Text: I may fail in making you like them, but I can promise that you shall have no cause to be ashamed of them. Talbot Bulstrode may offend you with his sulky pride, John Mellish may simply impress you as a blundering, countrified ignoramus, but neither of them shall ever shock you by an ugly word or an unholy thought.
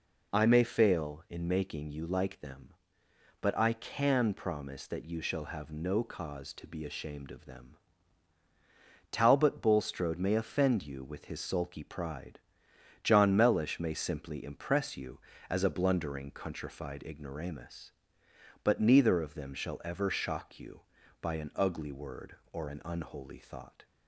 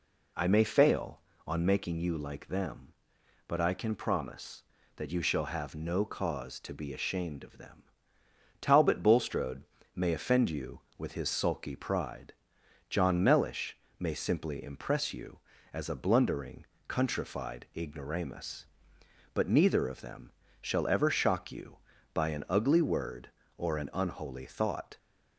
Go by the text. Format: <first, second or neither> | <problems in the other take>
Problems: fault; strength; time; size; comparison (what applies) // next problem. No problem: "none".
first | says "on" for "in"; at 1.4 s // pauses between "Bulstrode" and "may"; slight; at 9.6 s; 0.32 s long // pauses between "Mellish" and "may"; slight; at 13.7 s; 0.22 s long // pauses between "them" and "shall"; slight; at 20.3 s; 0.30 s long